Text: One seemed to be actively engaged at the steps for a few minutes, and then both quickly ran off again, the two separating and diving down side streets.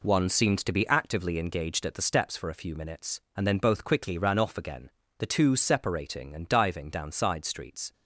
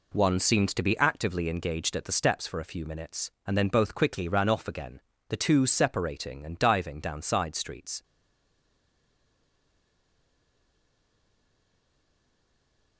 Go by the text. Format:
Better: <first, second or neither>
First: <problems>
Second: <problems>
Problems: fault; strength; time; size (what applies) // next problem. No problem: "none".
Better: first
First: none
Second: stays silent after the last word; strong; from 8.0 s on; 4.9 s long